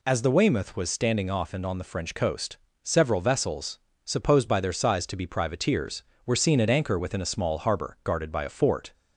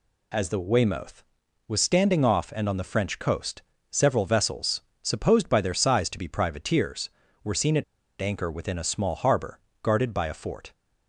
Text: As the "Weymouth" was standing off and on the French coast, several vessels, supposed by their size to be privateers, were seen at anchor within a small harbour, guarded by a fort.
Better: first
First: none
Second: pauses between "at" and "anchor"; at 7.8 s; 0.38 s long

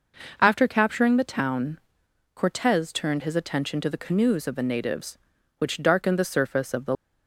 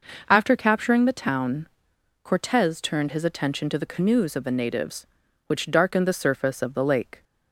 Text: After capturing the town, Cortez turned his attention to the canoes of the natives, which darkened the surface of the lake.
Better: second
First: stops before "lake"; at 6.9 s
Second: none

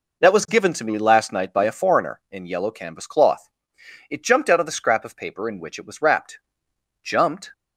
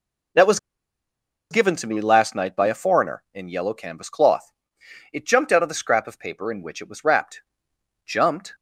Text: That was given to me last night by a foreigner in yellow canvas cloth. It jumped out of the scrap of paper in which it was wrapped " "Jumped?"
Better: first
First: none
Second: pauses between "was" and "given"; noticeable; at 0.5 s; 0.92 s long

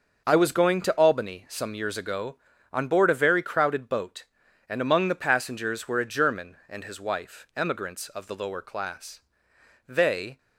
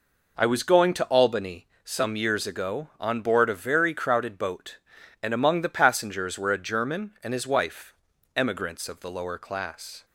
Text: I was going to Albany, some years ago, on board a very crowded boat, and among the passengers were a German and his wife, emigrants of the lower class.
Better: second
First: starts louder than the rest; noticeable; until 1.2 s; 6 dB // goes on to say "They"; from 9.8 s on; 0.52 s long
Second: none

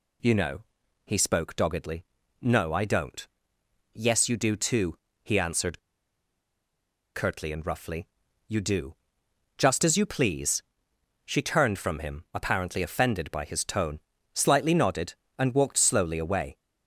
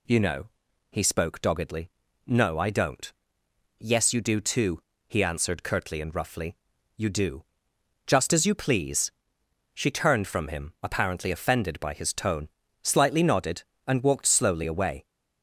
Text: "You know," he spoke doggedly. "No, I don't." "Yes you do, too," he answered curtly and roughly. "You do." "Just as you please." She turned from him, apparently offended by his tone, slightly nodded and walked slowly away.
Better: second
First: pauses between "answered" and "curtly"; strong; at 5.7 s; 1.3 s long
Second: none

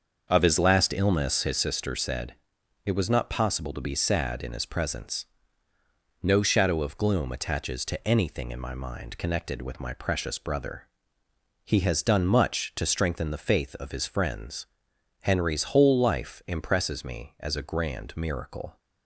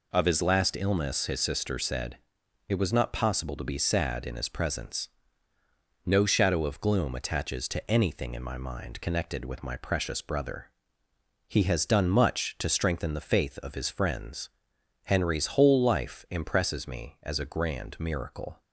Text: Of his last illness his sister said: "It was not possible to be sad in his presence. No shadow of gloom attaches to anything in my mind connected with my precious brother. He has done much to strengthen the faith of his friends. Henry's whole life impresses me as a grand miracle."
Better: second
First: starts louder than the rest; until 1.7 s; 6.5 dB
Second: none

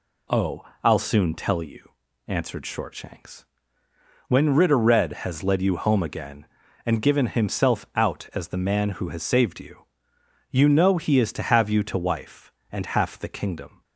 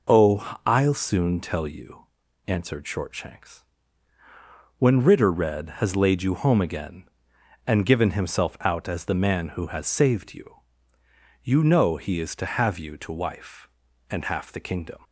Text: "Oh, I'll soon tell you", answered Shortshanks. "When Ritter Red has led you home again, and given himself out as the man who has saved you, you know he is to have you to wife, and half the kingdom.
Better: first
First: none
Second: says "laid" for "led"; at 5.9 s

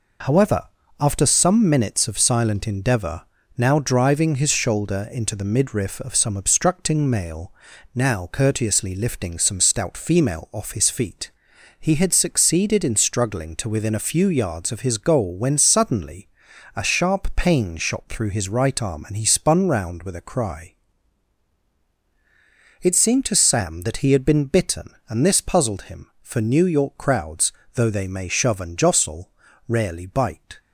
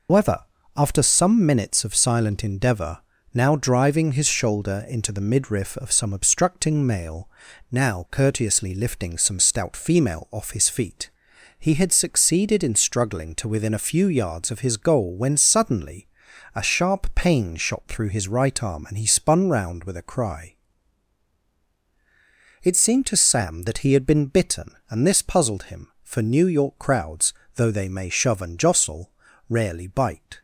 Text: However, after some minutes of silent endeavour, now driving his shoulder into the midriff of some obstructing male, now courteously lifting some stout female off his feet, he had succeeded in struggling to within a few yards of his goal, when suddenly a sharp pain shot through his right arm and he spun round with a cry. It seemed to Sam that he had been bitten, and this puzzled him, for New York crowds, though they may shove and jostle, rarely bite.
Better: first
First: pauses between "suddenly" and "a"; noticeable; at 16.2 s; 0.48 s long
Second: loses the start of "However"; at 0.0 s; 130 ms // pauses between "suddenly" and "a"; noticeable; at 16.0 s; 0.48 s long

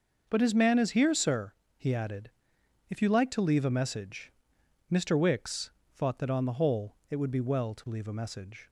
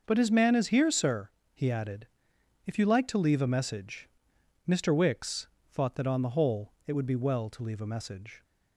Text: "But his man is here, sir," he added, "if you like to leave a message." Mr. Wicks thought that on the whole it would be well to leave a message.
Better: neither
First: starts louder than the rest; noticeable; until 1.3 s; 6 dB // pauses between "Wicks" and "thought"; slight; at 5.7 s; 0.22 s long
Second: starts louder than the rest; noticeable; until 1.0 s; 6 dB // pauses between "Wicks" and "thought"; slight; at 5.4 s; 0.22 s long

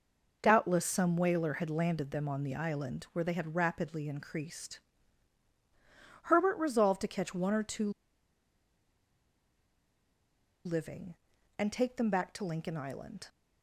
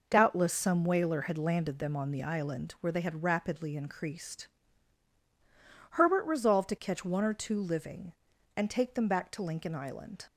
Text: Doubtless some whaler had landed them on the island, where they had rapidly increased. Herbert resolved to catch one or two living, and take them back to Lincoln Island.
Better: second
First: pauses between "two" and "living"; strong; at 7.8 s; 2.7 s long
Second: none

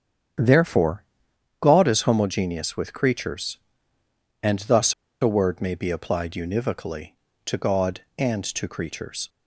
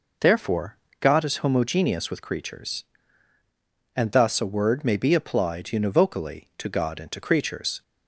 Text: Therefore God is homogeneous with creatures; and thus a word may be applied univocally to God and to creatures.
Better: second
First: starts louder than the rest; strong; until 1.9 s; 8.5 dB // pauses between "Therefore" and "God"; noticeable; at 1.0 s; 0.56 s long // pauses between "thus" and "a"; slight; at 4.9 s; 0.28 s long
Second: pauses between "Therefore" and "God"; slight; at 0.7 s; 0.24 s long

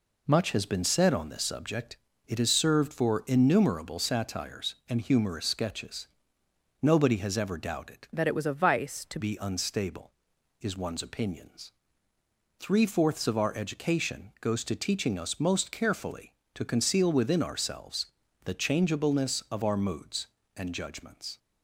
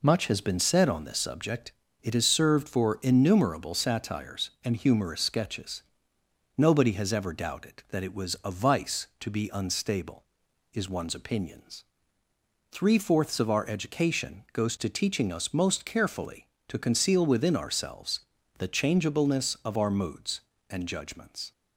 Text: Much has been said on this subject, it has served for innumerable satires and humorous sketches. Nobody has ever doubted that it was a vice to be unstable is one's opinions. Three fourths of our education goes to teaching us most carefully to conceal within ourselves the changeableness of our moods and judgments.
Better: second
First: changes voice from "that" to "to"; from 8.1 to 9.1 s; 1.0 s long // pauses between "ourselves" and "the"; at 18.0 s; 0.38 s long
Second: pauses between "ourselves" and "the"; at 18.1 s; 0.38 s long

